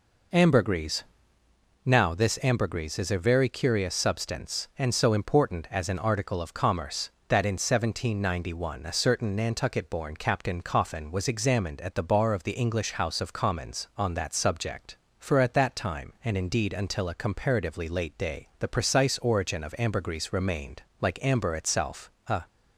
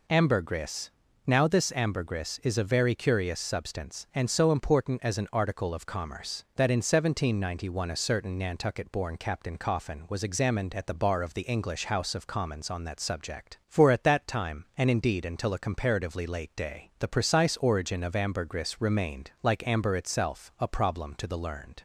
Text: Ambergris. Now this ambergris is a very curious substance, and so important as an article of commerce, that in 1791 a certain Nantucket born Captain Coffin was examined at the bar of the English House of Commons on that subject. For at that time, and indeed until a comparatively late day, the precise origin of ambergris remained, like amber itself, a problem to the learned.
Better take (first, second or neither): second